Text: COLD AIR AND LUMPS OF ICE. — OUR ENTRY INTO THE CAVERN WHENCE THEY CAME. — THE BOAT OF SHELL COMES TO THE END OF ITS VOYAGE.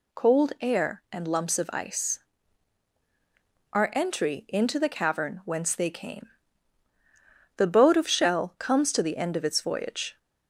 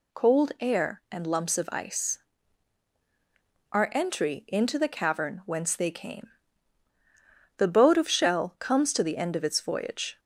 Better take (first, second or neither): neither